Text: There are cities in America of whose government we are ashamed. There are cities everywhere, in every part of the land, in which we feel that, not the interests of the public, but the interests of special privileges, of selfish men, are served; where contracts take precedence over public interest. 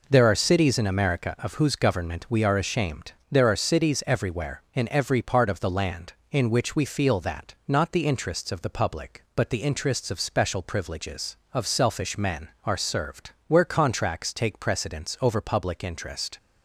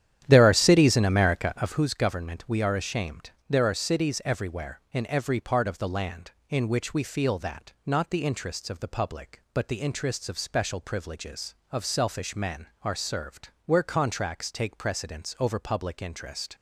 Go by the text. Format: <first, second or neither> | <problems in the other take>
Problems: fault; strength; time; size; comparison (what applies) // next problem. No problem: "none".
first | starts louder than the rest; strong; until 1.8 s; 10.5 dB